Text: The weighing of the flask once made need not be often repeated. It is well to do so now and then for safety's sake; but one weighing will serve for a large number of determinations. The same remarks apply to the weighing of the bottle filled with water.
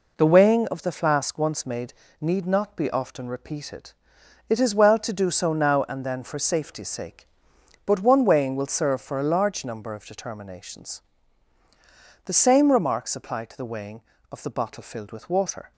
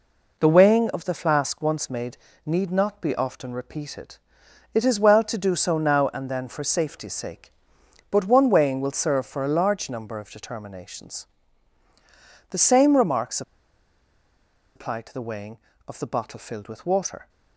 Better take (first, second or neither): first